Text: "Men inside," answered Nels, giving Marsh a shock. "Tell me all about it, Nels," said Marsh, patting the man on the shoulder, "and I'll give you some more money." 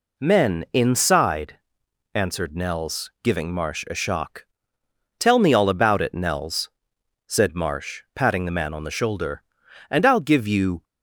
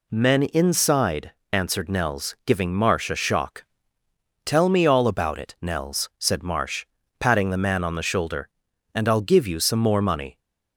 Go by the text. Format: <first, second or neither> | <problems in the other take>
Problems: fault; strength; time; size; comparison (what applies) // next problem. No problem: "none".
second | stops before "some more money"; at 10.8 s